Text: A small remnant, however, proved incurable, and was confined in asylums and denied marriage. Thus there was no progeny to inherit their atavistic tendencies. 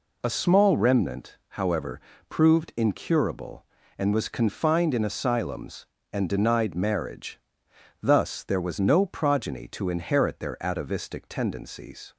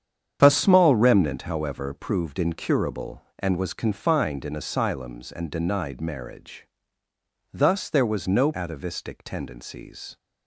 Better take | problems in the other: first | starts louder than the rest; strong; until 1.4 s; 8 dB // skips "progeny to inherit their"; at 8.5 s

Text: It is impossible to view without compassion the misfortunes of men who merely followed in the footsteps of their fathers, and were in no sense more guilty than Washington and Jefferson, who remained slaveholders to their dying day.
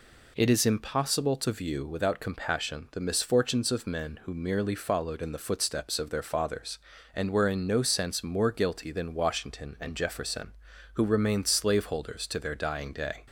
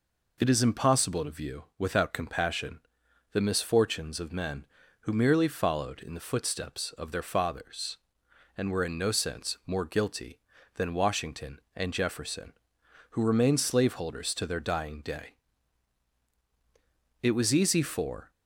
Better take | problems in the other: first | pauses between "compassion" and "the"; noticeable; at 2.7 s; 0.54 s long // goes on to say "It was easy for"; noticeable; from 17.2 s on; 1.1 s long

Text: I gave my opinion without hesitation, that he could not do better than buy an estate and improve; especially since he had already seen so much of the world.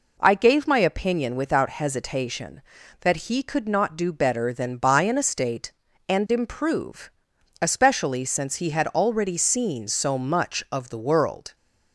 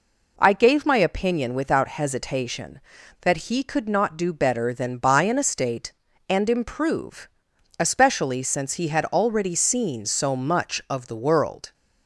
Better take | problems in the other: neither | none

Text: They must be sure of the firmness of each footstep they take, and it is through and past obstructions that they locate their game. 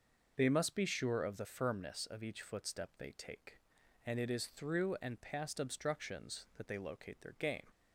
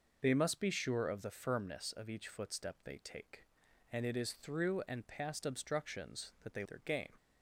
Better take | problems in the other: first | skips "locate"; at 6.6 s

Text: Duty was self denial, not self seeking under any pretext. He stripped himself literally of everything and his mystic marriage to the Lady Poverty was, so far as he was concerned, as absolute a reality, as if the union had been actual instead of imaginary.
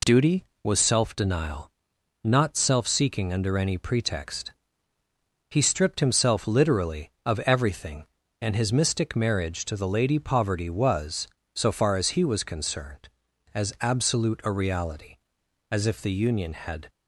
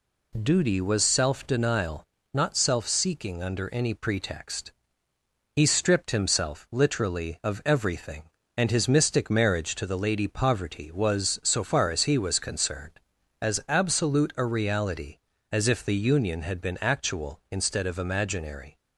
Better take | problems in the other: second | stops before "been actual instead of imaginary"; at 16.8 s

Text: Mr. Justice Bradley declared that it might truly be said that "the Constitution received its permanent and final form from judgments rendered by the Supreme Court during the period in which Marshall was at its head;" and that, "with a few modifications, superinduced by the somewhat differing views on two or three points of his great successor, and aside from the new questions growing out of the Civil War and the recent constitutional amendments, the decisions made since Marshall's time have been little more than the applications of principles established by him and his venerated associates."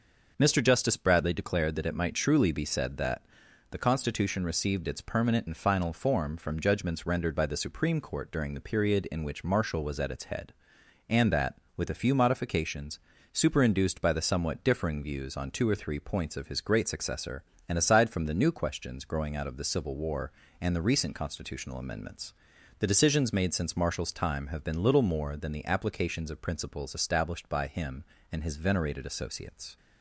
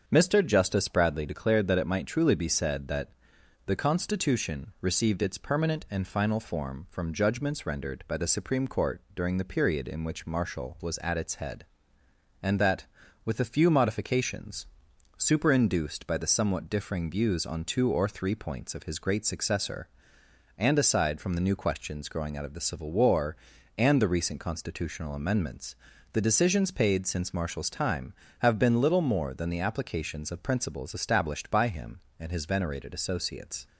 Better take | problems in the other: first | starts louder than the rest; until 1.0 s; 7 dB // pauses between "that" and "the"; noticeable; at 3.0 s; 0.56 s long; noticeable in the first // says "paid" for "made"; at 26.6 s

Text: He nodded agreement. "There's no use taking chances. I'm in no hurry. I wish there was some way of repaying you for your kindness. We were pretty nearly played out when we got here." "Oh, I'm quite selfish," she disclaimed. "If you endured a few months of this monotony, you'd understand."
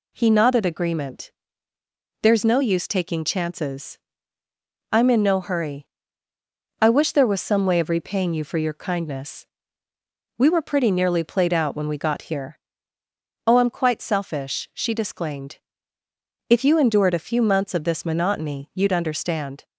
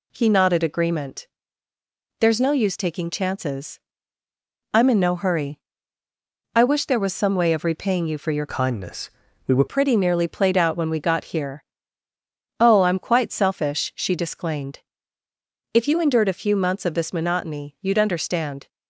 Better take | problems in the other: first | changes voice from "kindness" to "were"; from 8.4 to 9.6 s; 1.2 s long

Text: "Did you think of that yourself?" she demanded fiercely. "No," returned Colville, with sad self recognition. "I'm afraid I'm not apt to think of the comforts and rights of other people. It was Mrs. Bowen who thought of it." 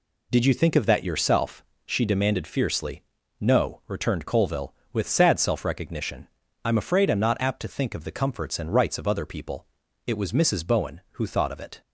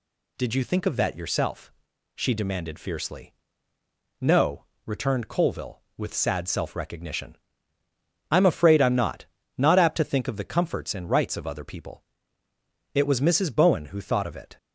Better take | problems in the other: first | says "not" twice; at 9.5 s

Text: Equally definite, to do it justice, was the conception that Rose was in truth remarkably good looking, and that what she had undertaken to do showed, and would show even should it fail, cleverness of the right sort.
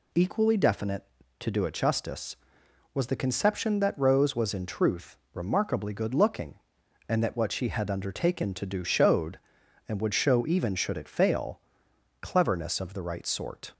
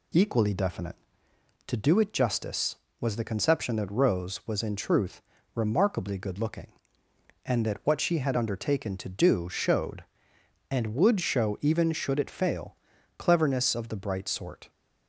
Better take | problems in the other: first | pauses between "truth" and "remarkably"; slight; at 5.2 s; 0.32 s long; slight in the first // says "bright" for "right"; at 13.9 s

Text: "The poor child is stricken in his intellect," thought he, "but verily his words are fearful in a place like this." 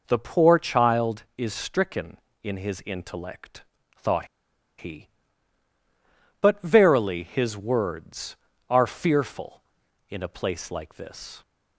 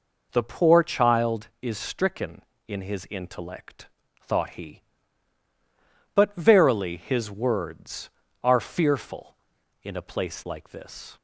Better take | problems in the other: second | pauses between "thought" and "he"; noticeable; at 4.2 s; 0.51 s long

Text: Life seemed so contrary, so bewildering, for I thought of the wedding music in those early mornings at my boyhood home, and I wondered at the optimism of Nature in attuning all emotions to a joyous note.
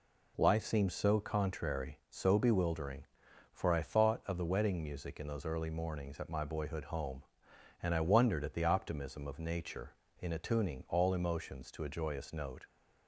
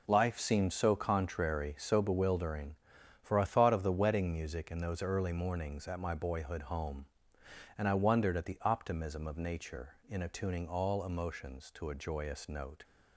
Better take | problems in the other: neither | none

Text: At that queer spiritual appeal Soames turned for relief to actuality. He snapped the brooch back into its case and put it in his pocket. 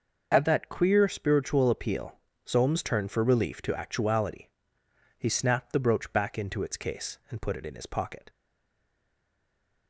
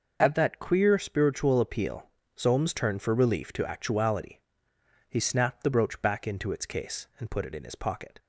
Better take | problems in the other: second | pauses between "appeal" and "Soames"; slight; at 2.1 s; 0.30 s long; slight in the second // stays silent after the last word; noticeable; from 8.2 s on; 1.6 s long

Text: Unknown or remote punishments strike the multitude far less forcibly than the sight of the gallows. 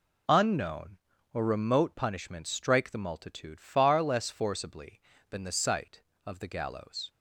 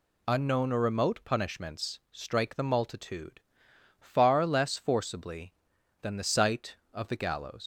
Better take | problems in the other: first | pauses between "multitude" and "far"; noticeable; at 3.4 s; 0.58 s long // leaves "gallows" unfinished; at 7.6 s; 110 ms

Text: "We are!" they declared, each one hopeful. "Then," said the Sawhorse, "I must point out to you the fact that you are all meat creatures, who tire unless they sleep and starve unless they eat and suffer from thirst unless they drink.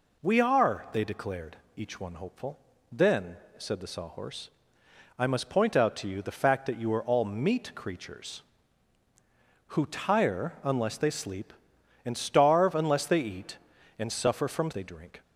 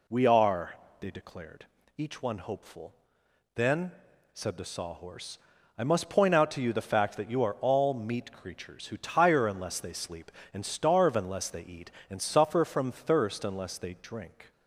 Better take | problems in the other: second | skips "thirst unless"; at 14.7 s

